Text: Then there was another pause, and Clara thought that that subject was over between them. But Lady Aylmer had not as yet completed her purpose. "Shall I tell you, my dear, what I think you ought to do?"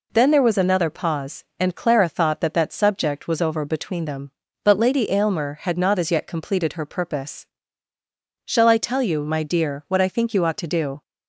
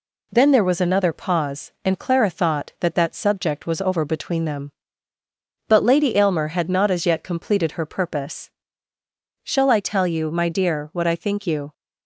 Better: first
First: none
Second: stops before "ought to do"; at 11.7 s

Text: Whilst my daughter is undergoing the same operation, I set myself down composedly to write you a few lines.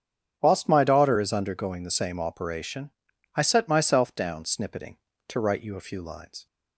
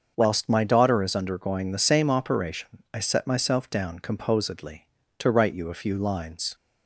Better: second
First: starts louder than the rest; strong; until 1.4 s; 8.5 dB // says "snippeting" for "composedly"; at 4.4 s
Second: starts louder than the rest; until 1.1 s; 6.5 dB

